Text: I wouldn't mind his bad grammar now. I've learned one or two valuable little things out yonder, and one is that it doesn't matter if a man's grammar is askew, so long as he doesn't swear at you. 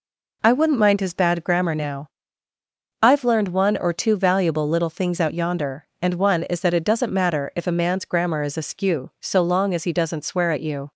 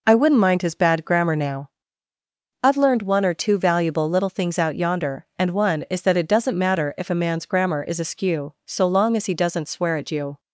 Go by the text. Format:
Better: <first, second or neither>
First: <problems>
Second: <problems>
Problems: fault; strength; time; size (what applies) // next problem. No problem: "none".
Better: neither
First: none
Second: none